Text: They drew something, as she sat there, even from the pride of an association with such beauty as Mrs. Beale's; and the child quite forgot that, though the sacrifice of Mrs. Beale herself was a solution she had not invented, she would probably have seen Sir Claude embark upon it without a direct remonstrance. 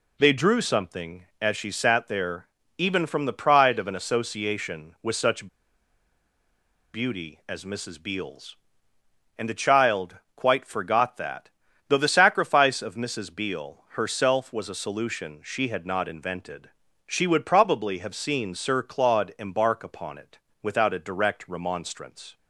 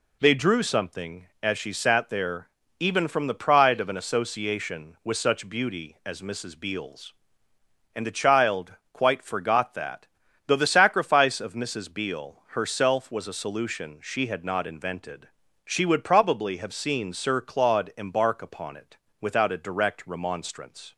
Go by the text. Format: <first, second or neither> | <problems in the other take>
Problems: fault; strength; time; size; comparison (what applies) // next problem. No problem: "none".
second | pauses between "such" and "beauty"; strong; at 5.4 s; 1.4 s long // pauses between "child" and "quite"; slight; at 10.1 s; 0.18 s long; slight in the second // pauses between "it" and "without"; slight; at 20.3 s; 0.24 s long; slight in the second